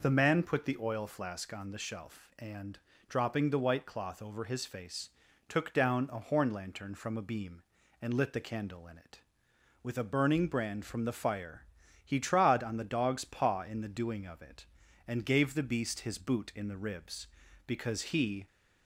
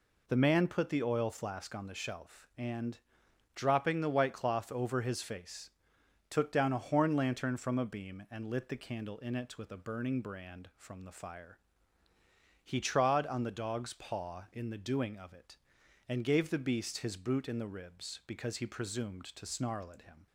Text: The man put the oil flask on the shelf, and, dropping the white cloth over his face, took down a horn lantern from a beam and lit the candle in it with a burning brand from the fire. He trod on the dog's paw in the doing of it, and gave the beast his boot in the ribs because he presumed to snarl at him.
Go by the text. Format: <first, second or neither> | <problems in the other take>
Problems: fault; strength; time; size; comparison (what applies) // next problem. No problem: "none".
second | stops before "presumed to snarl at him"; at 18.4 s